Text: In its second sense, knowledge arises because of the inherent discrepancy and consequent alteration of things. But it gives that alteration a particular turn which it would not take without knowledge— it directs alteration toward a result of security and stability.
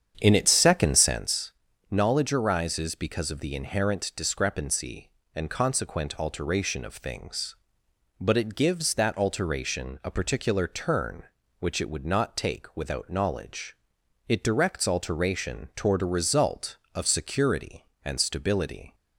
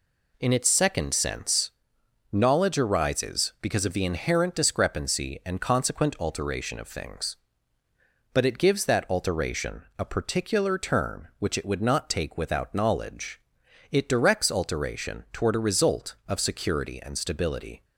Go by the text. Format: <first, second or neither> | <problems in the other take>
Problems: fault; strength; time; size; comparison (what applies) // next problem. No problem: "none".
second | starts louder than the rest; strong; until 1.2 s; 8 dB